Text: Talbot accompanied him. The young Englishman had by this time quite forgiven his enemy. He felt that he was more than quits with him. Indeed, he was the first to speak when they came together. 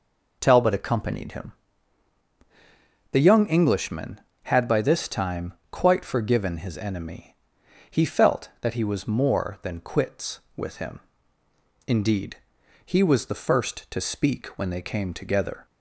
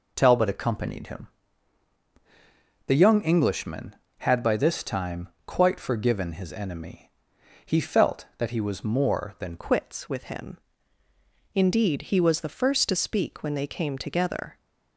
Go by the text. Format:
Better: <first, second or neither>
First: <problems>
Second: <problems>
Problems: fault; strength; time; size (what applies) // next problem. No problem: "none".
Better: first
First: pauses between "time" and "quite"; slight; at 5.5 s; 0.18 s long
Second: pauses between "time" and "quite"; slight; at 5.2 s; 0.18 s long // changes voice at "quits"; from 9.5 s on; 5.0 s long